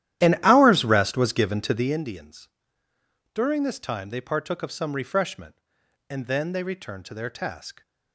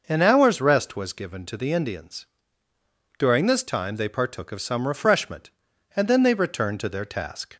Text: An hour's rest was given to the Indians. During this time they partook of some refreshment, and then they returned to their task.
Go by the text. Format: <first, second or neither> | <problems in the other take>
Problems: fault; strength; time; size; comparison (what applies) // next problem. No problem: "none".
second | starts louder than the rest; strong; until 2.0 s; 12.5 dB